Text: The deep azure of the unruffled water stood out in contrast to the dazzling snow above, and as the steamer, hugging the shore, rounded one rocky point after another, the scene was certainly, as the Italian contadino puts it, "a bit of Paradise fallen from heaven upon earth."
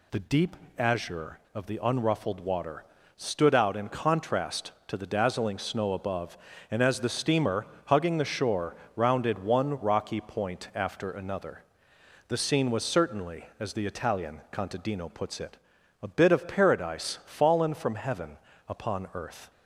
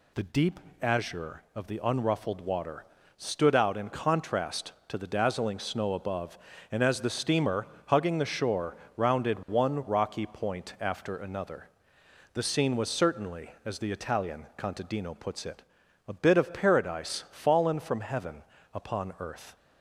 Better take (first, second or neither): neither